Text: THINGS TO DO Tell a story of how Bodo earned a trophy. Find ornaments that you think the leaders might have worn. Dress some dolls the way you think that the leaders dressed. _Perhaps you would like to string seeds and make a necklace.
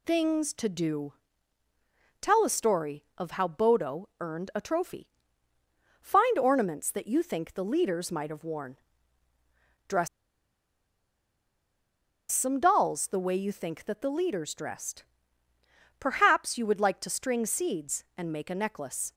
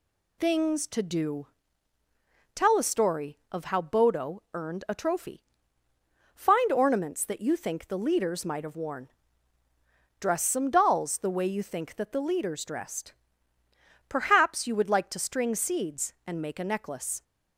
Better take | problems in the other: second | pauses between "DO" and "Tell"; at 1.1 s; 1.0 s long; also in the second // pauses between "Dress" and "some"; strong; at 10.0 s; 2.2 s long

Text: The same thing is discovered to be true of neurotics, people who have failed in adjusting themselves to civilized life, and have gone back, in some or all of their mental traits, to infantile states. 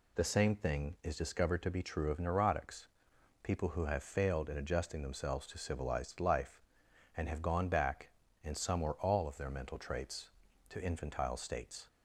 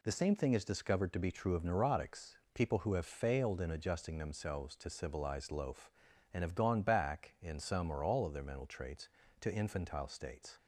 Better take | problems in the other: first | says "loaf" for "life"; at 5.5 s

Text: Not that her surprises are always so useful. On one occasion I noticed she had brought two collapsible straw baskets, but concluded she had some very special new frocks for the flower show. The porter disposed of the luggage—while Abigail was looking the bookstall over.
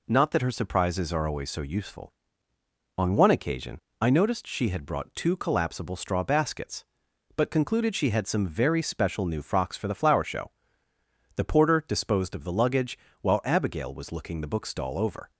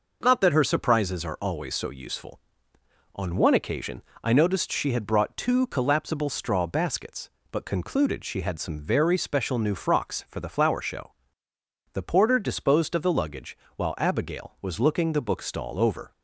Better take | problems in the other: neither | pauses between "occasion" and "I"; slight; the same in both

